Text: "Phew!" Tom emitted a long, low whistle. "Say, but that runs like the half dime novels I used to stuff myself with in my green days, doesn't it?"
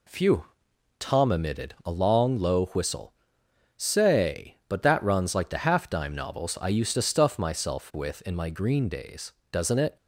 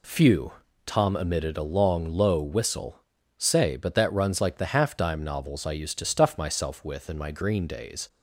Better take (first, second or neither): first